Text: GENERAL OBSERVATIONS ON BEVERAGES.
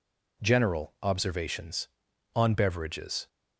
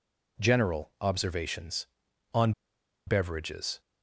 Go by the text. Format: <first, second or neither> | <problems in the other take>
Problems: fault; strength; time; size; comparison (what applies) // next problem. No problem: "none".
first | pauses between "ON" and "BEVERAGES"; noticeable; at 2.5 s; 0.55 s long